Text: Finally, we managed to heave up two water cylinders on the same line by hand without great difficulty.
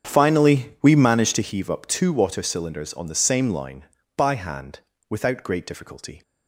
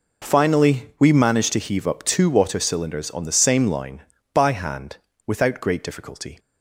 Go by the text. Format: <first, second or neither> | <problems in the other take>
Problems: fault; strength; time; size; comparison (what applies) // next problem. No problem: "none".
second | starts louder than the rest; strong; until 1.6 s; 7 dB // pauses between "hand" and "without"; slight; at 4.7 s; 0.30 s long; slight in the second